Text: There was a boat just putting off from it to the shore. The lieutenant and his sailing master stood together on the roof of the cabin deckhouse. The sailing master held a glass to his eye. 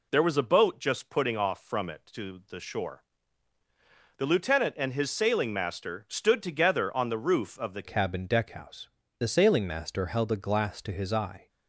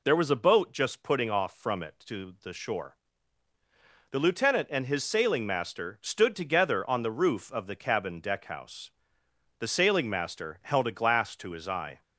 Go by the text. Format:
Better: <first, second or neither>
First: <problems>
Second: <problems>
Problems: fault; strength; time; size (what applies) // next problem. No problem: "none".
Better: second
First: changes voice at "cabin"; from 7.8 s on; 3.6 s long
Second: none